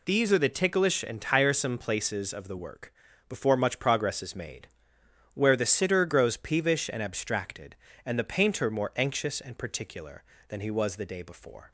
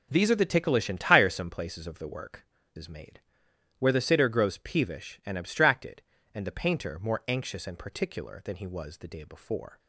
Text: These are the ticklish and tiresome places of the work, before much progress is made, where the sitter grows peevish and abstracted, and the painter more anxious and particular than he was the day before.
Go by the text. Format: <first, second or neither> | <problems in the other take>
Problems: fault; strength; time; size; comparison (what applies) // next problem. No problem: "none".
first | skips "before much progress"; at 2.6 s